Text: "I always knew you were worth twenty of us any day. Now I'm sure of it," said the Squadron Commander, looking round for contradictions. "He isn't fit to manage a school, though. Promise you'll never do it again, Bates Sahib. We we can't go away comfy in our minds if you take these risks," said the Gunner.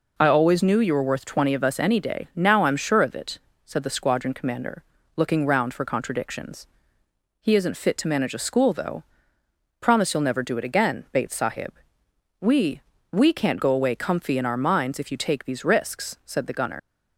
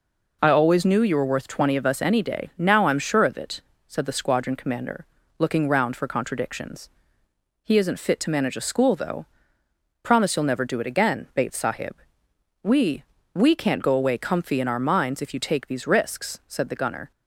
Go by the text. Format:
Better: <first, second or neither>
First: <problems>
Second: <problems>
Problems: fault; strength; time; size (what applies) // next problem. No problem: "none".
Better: second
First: pauses between "We" and "we"; slight; at 12.8 s; 0.32 s long // leaves "Gunner" unfinished; at 16.7 s; 85 ms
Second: pauses between "We" and "we"; slight; at 13.0 s; 0.32 s long